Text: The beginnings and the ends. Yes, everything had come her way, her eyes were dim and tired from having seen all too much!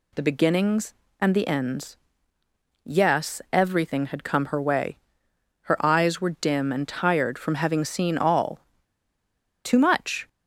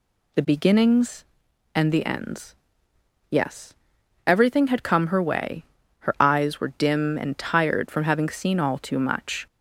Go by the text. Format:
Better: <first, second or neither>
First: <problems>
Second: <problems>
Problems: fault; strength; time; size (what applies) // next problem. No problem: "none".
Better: second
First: pauses between "all" and "too"; at 8.5 s; 1.0 s long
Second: none